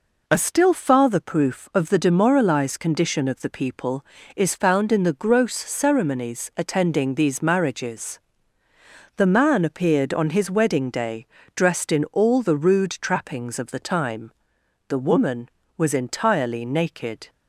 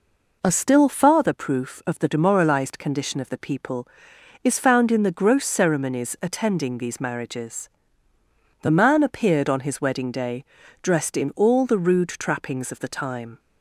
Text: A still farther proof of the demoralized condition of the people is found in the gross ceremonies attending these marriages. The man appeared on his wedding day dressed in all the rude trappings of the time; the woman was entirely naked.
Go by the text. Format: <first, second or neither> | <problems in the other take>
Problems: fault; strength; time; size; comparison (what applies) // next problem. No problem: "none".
first | pauses between "day" and "dressed"; slight; at 10.4 s; 0.36 s long; slight in the first // stops before "the woman was entirely naked"; at 13.3 s